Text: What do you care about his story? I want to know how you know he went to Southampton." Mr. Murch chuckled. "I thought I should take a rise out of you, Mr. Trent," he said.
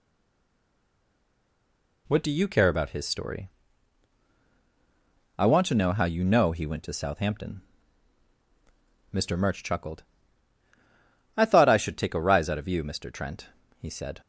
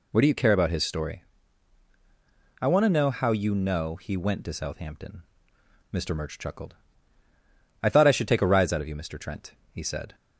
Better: second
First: stays silent before the first word; noticeable; until 2.0 s; 2.0 s long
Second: none

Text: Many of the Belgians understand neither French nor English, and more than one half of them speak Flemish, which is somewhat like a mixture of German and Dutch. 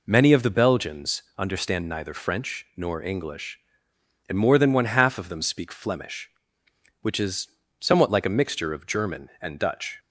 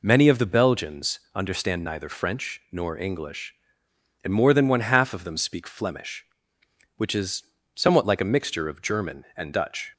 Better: neither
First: pauses between "Belgians" and "understand"; slight; at 1.2 s; 0.16 s long // pauses between "is" and "somewhat"; slight; at 7.4 s; 0.32 s long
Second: pauses between "Belgians" and "understand"; slight; at 1.1 s; 0.16 s long // pauses between "is" and "somewhat"; slight; at 7.4 s; 0.32 s long

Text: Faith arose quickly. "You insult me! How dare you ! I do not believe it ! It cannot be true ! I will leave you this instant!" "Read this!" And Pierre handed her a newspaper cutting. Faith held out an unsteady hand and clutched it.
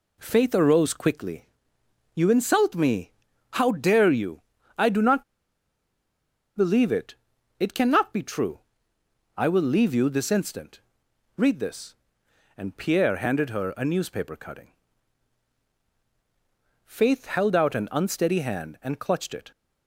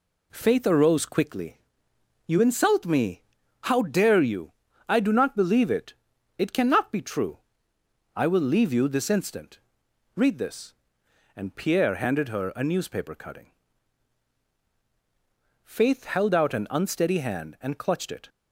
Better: second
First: pauses between "not" and "believe"; strong; at 5.2 s; 1.3 s long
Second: none

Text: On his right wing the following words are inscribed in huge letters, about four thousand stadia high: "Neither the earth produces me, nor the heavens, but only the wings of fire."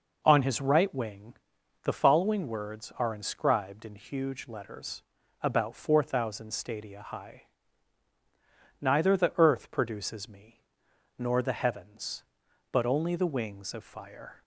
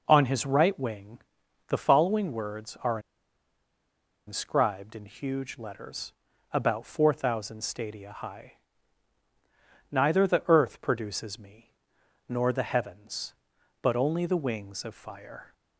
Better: first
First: pauses between "wing" and "the"; noticeable; at 1.3 s; 0.52 s long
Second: pauses between "wing" and "the"; noticeable; at 1.1 s; 0.52 s long // pauses between "are" and "inscribed"; strong; at 2.9 s; 1.2 s long

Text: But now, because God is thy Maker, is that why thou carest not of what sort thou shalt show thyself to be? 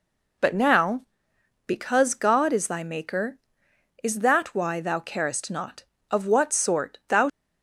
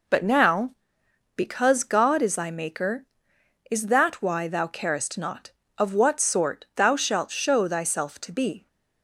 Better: second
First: stops before "shalt show thyself to be"; at 7.2 s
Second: none

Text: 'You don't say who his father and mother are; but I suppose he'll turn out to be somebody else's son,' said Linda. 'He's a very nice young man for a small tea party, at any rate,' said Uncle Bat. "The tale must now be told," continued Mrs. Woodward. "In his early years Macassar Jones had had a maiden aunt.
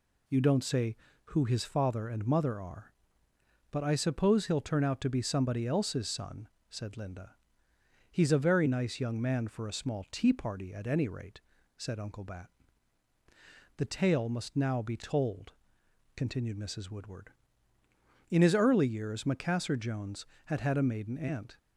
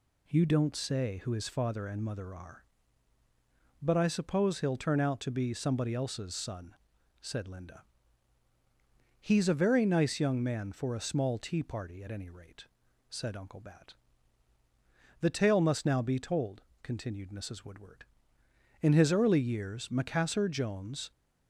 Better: first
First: none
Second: stops before "had had a maiden aunt"; at 21.1 s

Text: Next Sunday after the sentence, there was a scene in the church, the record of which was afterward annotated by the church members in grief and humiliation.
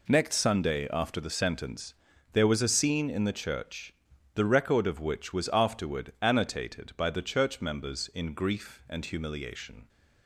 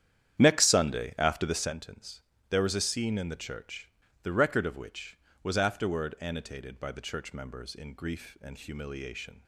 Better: first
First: none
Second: starts louder than the rest; strong; until 1.7 s; 10 dB

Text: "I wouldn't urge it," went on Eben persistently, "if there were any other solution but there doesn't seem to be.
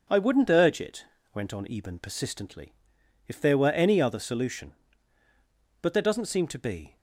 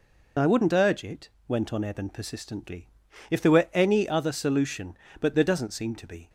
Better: first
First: none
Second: loses the start of "I"; at 0.3 s; 35 ms

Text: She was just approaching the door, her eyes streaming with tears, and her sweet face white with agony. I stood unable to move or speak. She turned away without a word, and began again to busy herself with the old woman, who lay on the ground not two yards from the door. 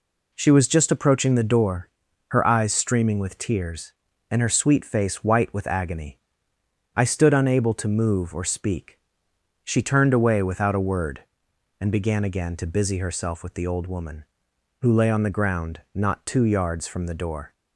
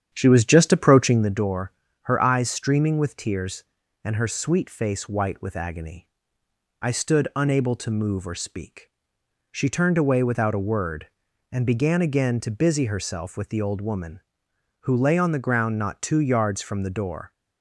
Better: first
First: none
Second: starts louder than the rest; strong; until 1.3 s; 9 dB

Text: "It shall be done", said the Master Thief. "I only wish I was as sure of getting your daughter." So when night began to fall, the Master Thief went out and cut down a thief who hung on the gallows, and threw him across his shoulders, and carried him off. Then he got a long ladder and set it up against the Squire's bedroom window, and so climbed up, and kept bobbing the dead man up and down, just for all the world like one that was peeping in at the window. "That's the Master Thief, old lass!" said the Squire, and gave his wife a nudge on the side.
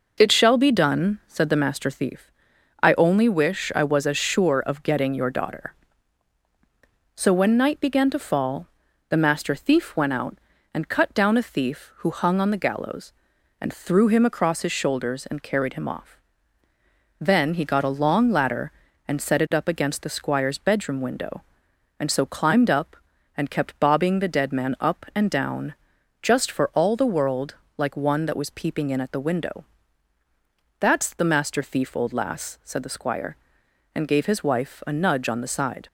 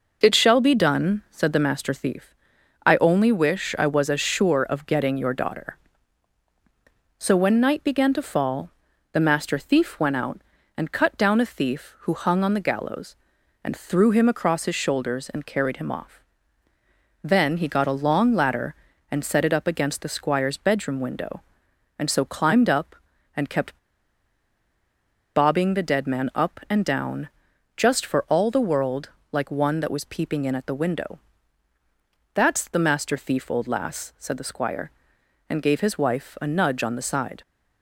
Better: first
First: pauses between "world" and "like"; slight; at 27.5 s; 0.22 s long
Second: pauses between "kept" and "bobbing"; strong; at 23.7 s; 1.5 s long // pauses between "world" and "like"; slight; at 29.0 s; 0.22 s long

